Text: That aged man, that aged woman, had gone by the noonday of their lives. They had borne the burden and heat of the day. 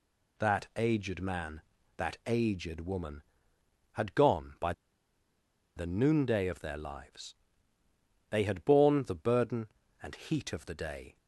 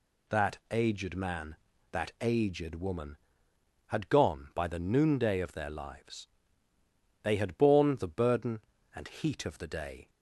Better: second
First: pauses between "by" and "the"; at 4.7 s; 1.0 s long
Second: none

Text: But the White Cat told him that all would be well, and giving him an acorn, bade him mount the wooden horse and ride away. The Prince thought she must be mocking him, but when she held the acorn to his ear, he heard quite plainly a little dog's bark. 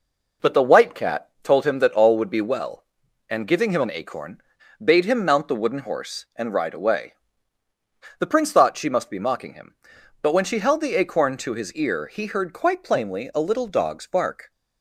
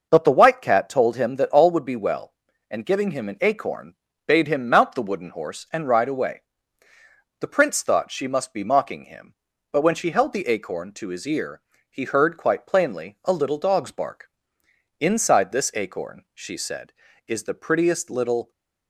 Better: first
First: none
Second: goes on to say "Inside this acorn she said is the prettiest little"; strong; from 14.9 s on; 3.5 s long

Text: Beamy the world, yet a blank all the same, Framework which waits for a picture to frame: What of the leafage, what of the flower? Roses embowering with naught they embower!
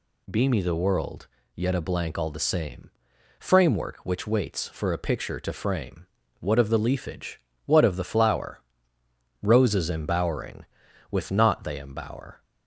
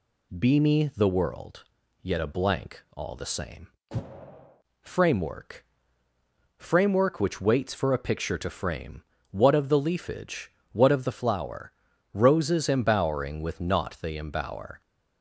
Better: first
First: none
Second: pauses between "blank" and "all"; slight; at 2.8 s; 0.16 s long // says "Framework" twice; at 6.5 s

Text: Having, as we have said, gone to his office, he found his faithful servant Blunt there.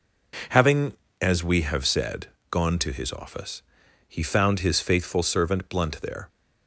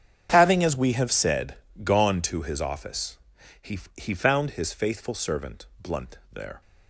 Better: first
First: none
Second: starts louder than the rest; strong; until 1.3 s; 8 dB // says "he" twice; at 3.9 s // pauses between "servant" and "Blunt"; slight; at 5.6 s; 0.16 s long

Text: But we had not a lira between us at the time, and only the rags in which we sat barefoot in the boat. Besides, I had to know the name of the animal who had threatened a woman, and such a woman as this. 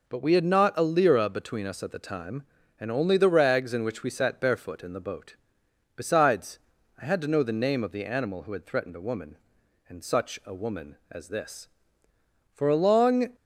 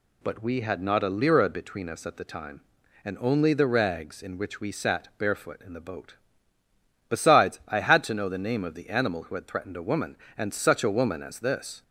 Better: second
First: goes on to say "For a long"; noticeable; from 12.5 s on; 0.80 s long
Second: none

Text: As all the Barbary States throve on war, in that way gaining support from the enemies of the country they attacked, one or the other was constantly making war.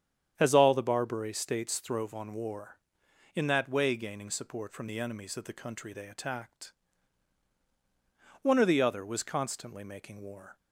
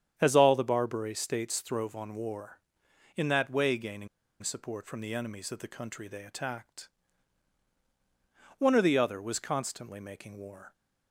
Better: first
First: starts louder than the rest; strong; until 1.3 s; 8.5 dB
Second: starts louder than the rest; strong; until 1.1 s; 9 dB // pauses between "gaining" and "support"; slight; at 4.0 s; 0.34 s long

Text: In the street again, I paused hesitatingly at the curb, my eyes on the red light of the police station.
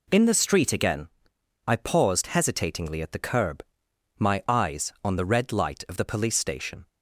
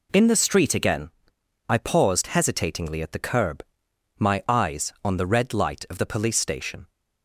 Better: neither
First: none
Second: none

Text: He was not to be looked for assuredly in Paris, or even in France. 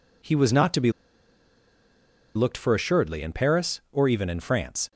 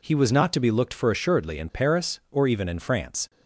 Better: second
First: pauses between "be" and "looked"; strong; at 0.9 s; 1.4 s long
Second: none

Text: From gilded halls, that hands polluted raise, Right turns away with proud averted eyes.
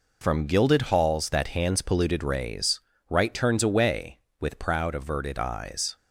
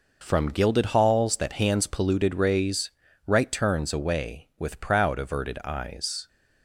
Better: neither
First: none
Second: none

